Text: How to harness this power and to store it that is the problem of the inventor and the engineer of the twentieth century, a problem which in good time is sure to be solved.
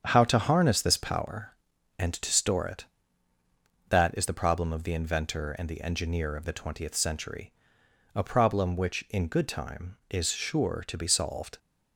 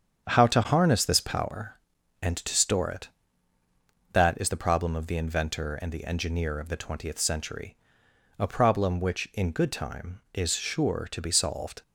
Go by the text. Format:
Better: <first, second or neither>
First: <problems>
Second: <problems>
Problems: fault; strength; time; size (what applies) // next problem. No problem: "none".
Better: neither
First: starts louder than the rest; strong; until 1.0 s; 8 dB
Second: starts louder than the rest; strong; until 1.3 s; 8 dB